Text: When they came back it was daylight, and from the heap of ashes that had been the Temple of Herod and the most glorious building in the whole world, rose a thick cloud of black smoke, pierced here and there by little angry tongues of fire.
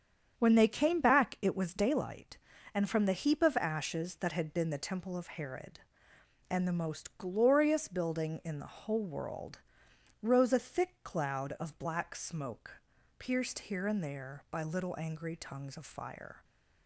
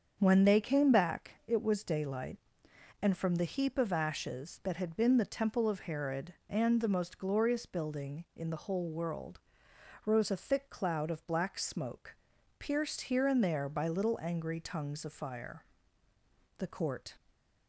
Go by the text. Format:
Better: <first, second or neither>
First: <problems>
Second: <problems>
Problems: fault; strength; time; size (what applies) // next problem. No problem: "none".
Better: first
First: starts louder than the rest; strong; until 1.3 s; 8 dB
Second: starts louder than the rest; until 1.2 s; 7 dB // goes on to say "The Court"; noticeable; from 16.5 s on; 0.62 s long